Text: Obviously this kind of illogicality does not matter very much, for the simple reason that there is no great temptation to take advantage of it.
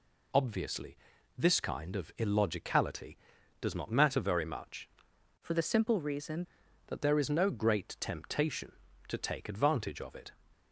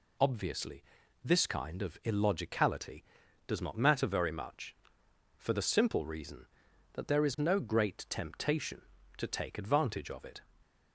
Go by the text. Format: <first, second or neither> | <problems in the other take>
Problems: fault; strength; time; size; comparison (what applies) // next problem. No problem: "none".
second | pauses between "Obviously" and "this"; at 0.9 s; 0.42 s long; also in the second // changes voice from "for" to "reason"; from 5.3 to 6.4 s; 1.1 s long